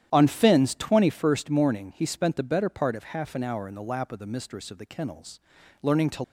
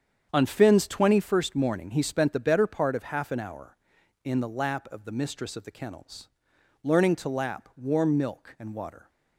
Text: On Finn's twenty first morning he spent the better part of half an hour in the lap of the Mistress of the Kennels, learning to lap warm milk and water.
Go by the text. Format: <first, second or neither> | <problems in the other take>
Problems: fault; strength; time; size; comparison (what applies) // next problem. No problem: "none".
second | starts louder than the rest; strong; until 1.1 s; 10.5 dB; strong in the second // stops before "lap warm milk and water"; at 6.2 s